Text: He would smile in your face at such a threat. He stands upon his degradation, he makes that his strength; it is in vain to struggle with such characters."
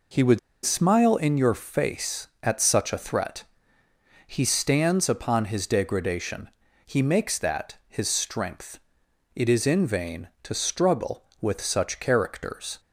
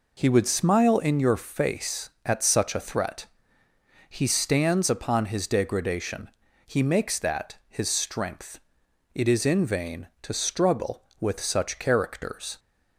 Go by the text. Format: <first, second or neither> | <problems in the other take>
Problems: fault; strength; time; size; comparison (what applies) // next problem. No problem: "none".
second | pauses between "would" and "smile"; slight; at 0.3 s; 0.26 s long